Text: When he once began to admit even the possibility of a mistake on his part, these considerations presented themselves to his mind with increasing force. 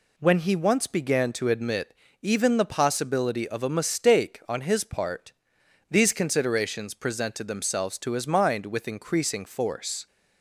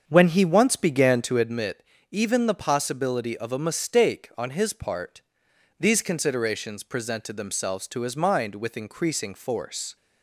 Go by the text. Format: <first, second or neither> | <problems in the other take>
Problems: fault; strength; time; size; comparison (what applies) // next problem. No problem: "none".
first | starts louder than the rest; until 1.5 s; 7 dB // pauses between "admit" and "even"; slight; at 1.8 s; 0.28 s long; slight in the first